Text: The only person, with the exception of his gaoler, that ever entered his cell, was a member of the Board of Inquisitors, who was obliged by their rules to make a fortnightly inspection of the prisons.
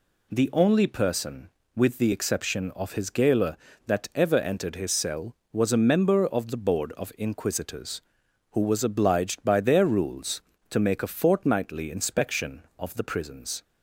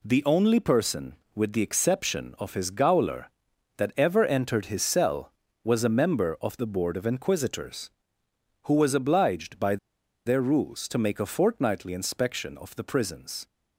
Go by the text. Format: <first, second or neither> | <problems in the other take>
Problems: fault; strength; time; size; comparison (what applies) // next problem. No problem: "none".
first | pauses between "by" and "their"; noticeable; at 9.7 s; 0.49 s long